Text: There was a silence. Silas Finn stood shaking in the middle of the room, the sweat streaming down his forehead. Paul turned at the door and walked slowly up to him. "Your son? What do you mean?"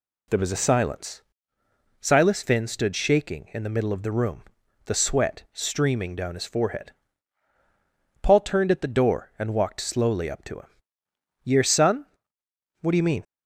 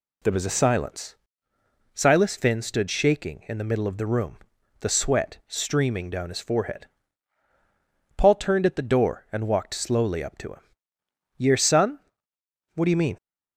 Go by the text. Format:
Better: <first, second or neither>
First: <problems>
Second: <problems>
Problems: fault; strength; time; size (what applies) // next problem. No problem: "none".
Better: neither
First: none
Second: none